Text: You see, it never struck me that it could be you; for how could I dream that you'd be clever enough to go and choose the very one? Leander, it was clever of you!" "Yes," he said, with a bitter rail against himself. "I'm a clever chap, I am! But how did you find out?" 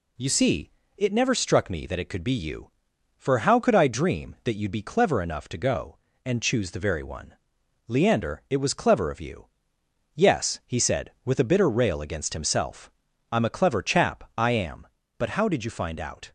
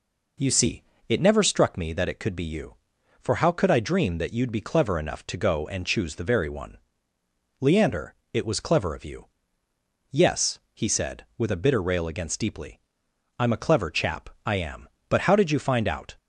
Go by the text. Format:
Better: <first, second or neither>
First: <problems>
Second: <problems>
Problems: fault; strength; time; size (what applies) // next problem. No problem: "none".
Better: first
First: none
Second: says "deeply" for "himself"; at 12.3 s